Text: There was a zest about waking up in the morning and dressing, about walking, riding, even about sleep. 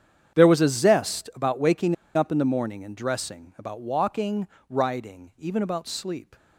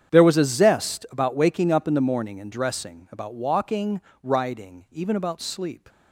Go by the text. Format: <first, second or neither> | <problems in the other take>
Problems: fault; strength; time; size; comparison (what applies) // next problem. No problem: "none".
second | starts louder than the rest; strong; until 1.4 s; 8.5 dB; strong in the second // pauses between "waking" and "up"; slight; at 1.9 s; 0.20 s long